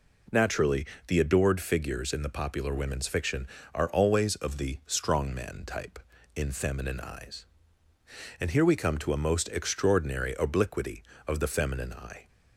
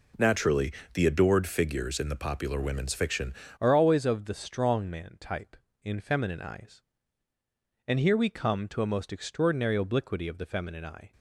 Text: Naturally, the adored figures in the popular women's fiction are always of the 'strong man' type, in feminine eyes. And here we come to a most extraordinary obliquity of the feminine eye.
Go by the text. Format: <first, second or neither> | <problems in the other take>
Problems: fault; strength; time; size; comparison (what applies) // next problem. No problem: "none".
first | changes voice at "are"; from 3.5 s on; 7.6 s long